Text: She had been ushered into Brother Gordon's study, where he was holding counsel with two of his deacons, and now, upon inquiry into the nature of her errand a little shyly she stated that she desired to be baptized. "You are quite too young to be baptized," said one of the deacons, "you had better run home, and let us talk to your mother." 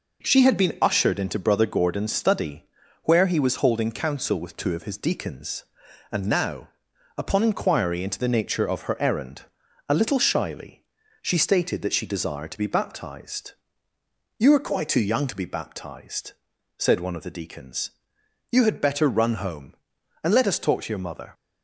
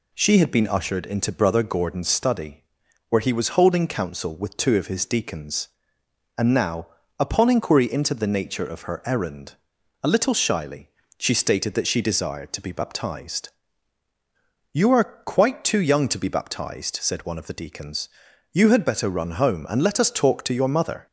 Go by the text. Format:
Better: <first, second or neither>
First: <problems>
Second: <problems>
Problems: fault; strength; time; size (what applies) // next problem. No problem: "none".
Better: neither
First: pauses between "errand" and "a"; noticeable; at 9.4 s; 0.46 s long // pauses between "shyly" and "she"; at 10.8 s; 0.40 s long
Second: pauses between "errand" and "a"; noticeable; at 9.5 s; 0.48 s long // pauses between "shyly" and "she"; slight; at 10.8 s; 0.30 s long